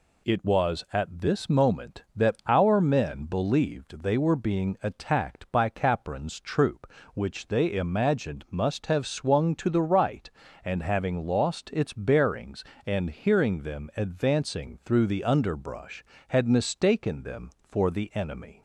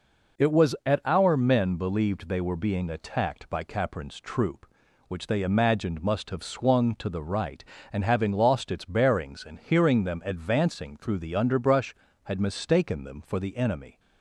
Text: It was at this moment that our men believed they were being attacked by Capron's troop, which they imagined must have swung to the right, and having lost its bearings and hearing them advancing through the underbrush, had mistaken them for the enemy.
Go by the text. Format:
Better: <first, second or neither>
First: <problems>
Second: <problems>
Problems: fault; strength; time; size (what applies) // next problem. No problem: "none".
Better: first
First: none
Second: skips "this moment that"; at 1.0 s